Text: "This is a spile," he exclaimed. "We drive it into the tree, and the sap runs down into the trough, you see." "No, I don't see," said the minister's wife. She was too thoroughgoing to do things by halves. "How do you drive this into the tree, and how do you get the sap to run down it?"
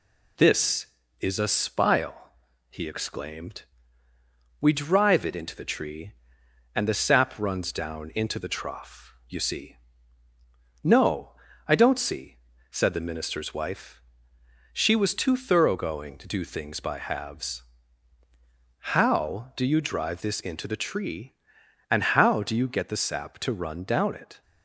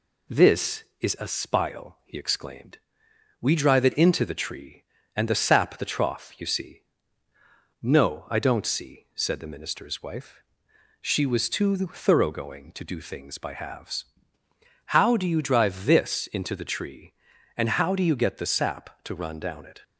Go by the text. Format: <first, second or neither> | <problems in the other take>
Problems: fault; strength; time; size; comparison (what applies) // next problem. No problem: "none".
first | skips "runs down into"; at 5.7 s